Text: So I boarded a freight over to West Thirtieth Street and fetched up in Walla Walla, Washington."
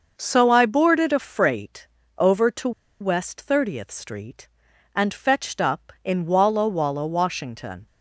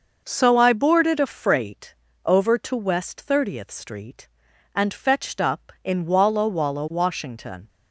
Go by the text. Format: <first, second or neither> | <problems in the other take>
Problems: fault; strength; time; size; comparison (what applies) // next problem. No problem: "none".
second | starts louder than the rest; noticeable; until 1.1 s; 6 dB; noticeable in the second // pauses between "freight" and "over"; slight; at 1.8 s; 0.30 s long; slight in the second // pauses between "to" and "West"; slight; at 2.7 s; 0.30 s long